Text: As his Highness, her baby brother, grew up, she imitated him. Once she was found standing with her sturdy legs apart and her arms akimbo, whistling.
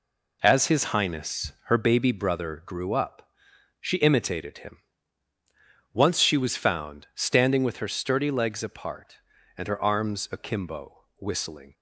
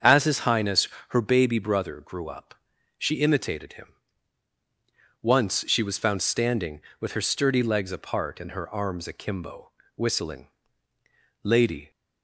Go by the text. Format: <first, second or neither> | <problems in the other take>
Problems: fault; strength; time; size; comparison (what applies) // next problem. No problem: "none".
first | starts louder than the rest; strong; until 1.2 s; 7.5 dB // goes on to say "Lady"; slight; from 11.4 s on; 0.48 s long